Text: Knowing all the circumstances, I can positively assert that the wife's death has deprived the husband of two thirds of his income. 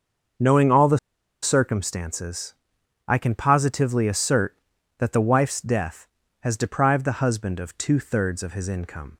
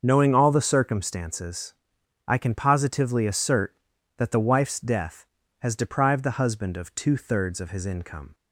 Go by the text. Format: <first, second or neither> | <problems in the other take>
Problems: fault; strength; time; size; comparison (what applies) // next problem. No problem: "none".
second | starts louder than the rest; until 1.8 s; 6.5 dB; also in the second // pauses between "the" and "circumstances"; at 0.9 s; 0.45 s long